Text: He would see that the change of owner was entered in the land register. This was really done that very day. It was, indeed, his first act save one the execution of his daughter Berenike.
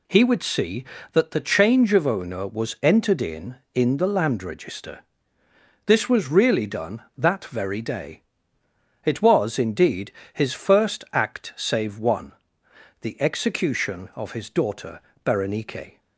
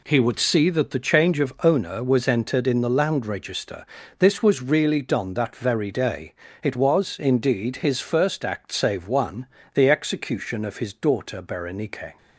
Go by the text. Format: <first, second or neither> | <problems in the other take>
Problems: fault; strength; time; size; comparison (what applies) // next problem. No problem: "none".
second | says "in" twice; at 3.7 s // pauses between "one" and "the"; noticeable; at 12.3 s; 0.68 s long; slight in the second // pauses between "daughter" and "Berenike"; slight; at 14.9 s; 0.26 s long